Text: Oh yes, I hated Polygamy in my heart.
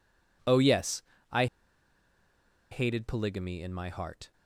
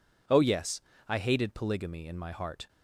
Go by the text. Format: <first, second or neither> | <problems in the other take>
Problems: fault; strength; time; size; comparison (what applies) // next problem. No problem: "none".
second | pauses between "I" and "hated"; strong; at 1.4 s; 1.2 s long